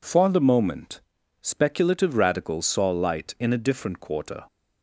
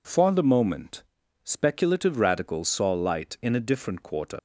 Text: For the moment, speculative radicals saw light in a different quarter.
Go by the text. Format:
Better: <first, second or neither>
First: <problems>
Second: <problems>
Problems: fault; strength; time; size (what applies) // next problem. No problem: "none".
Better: first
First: none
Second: leaves "quarter" unfinished; at 4.3 s; 95 ms